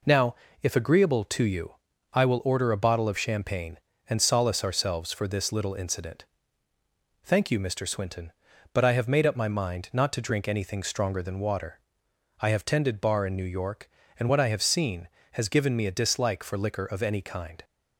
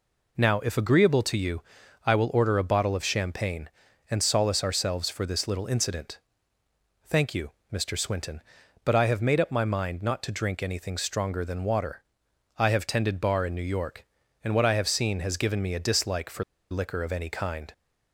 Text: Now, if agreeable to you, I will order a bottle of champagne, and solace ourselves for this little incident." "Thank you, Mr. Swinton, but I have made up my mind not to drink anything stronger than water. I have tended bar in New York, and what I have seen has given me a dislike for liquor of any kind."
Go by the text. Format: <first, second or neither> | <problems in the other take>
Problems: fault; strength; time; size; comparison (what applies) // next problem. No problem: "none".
first | pauses between "for" and "liquor"; slight; at 16.4 s; 0.27 s long